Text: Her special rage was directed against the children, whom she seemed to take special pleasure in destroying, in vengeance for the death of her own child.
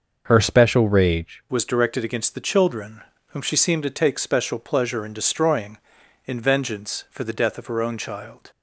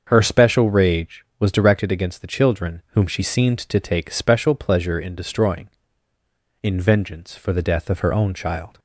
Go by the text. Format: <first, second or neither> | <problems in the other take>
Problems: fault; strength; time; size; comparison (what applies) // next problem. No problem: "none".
second | starts louder than the rest; noticeable; until 1.2 s; 6 dB; also in the second // changes voice at "was"; from 1.4 s on; 7.1 s long